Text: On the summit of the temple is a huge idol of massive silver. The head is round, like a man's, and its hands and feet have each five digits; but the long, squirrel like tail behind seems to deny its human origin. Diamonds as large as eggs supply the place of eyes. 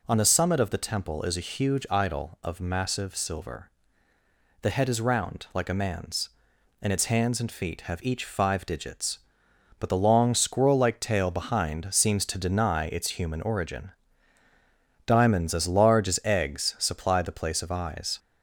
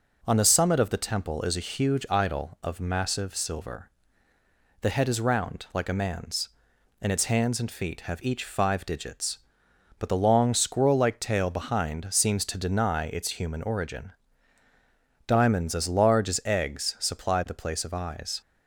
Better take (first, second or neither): second